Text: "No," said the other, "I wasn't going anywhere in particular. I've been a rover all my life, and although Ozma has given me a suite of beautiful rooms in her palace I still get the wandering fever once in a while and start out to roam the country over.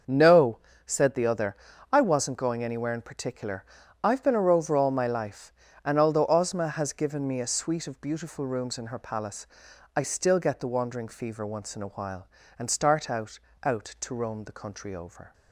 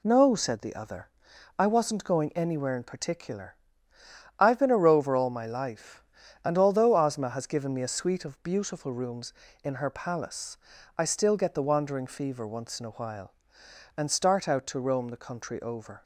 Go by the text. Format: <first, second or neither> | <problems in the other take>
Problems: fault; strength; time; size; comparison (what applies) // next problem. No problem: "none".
second | starts louder than the rest; until 1.3 s; 6.5 dB // pauses between "palace" and "I"; noticeable; at 9.4 s; 0.50 s long; also in the second // says "out" twice; at 13.6 s